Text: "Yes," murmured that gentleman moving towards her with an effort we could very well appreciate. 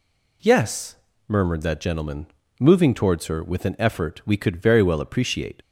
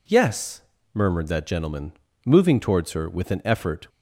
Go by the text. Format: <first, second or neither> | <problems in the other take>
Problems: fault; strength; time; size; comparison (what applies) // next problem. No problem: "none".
first | pauses between "gentleman" and "moving"; slight; at 1.9 s; 0.34 s long; slight in the first // stops before "we could very well appreciate"; at 3.8 s